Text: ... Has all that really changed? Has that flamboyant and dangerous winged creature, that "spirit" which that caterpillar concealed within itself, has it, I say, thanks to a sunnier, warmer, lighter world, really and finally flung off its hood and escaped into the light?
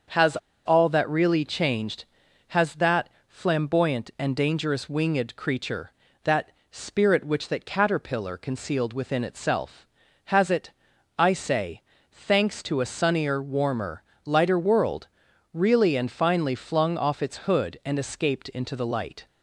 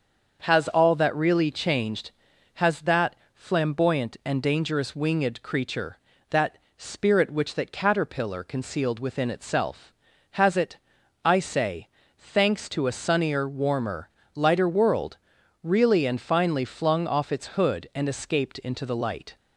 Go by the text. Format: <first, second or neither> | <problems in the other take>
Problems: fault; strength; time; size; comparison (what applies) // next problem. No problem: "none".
second | starts louder than the rest; until 1.4 s; 6.5 dB; also in the second // pauses between "Has" and "all"; slight; at 0.3 s; 0.28 s long // pauses between "that" and "flamboyant"; slight; at 3.0 s; 0.20 s long; slight in the second // pauses between "that" and "spirit"; slight; at 6.5 s; 0.22 s long; slight in the second